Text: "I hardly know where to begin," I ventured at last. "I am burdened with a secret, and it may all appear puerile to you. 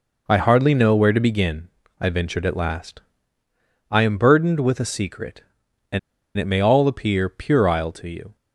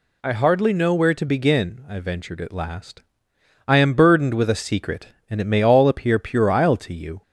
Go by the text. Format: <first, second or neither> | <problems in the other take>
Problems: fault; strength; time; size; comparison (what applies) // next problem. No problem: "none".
second | pauses between "and" and "it"; at 5.9 s; 0.37 s long